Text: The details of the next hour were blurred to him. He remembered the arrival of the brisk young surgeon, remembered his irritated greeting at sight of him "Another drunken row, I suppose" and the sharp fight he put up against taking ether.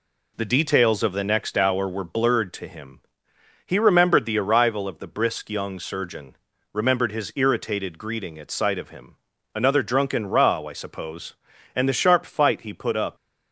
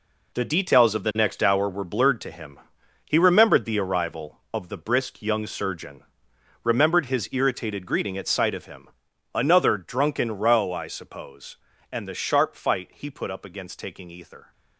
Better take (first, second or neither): second